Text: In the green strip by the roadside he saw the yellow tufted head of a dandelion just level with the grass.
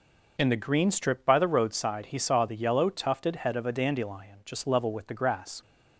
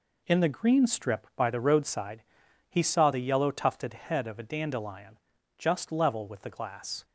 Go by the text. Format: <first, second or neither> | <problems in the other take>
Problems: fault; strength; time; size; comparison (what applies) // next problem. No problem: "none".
first | pauses between "roadside" and "he"; noticeable; at 2.2 s; 0.46 s long // pauses between "dandelion" and "just"; at 5.1 s; 0.40 s long // says "glass" for "grass"; at 6.5 s